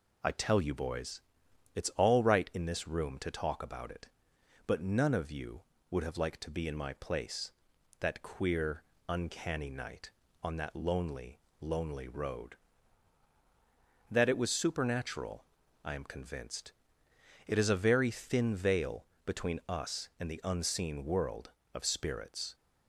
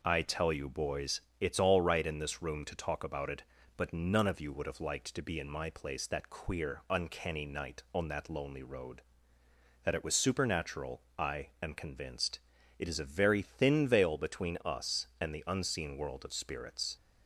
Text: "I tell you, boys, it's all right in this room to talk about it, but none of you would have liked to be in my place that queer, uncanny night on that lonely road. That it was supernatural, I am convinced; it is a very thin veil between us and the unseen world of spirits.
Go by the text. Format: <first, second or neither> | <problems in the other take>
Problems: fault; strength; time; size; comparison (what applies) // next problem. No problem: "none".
second | says "lonely" twice; at 11.6 s // pauses between "veil" and "between"; slight; at 19.0 s; 0.20 s long